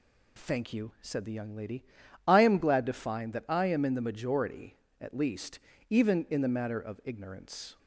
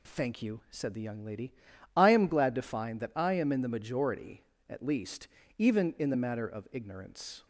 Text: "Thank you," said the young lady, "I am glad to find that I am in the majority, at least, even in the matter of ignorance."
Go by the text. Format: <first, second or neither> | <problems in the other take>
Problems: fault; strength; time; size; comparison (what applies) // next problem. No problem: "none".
neither | none